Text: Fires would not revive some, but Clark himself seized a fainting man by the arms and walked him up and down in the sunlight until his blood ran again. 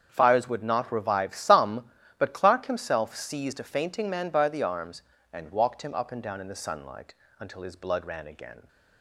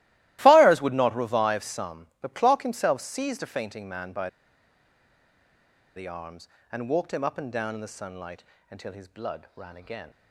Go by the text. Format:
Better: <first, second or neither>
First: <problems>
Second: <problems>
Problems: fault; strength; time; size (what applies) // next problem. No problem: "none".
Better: first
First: starts louder than the rest; strong; until 1.1 s; 8 dB // pauses between "sunlight" and "until"; slight; at 7.1 s; 0.26 s long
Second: starts louder than the rest; strong; until 1.4 s; 16.5 dB // pauses between "by" and "the"; strong; at 4.2 s; 1.6 s long // pauses between "sunlight" and "until"; slight; at 8.4 s; 0.26 s long